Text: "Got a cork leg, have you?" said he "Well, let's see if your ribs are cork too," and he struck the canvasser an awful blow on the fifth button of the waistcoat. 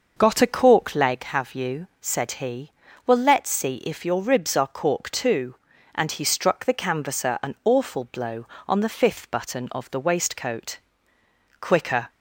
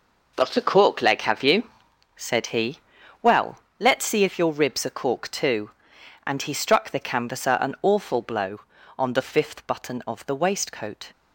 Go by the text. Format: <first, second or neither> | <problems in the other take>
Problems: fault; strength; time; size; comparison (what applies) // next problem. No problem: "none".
second | pauses between "he" and "Well"; slight; at 2.7 s; 0.34 s long; also in the second // goes on to say "Quicker"; from 11.5 s on; 0.50 s long